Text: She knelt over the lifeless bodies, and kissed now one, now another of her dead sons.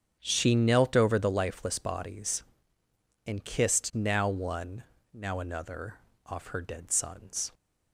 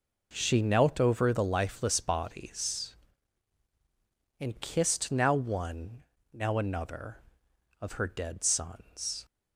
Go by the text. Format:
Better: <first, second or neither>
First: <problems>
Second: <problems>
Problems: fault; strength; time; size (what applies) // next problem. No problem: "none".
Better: second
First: starts louder than the rest; strong; until 1.2 s; 7.5 dB // says "off" for "of"; at 6.2 s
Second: none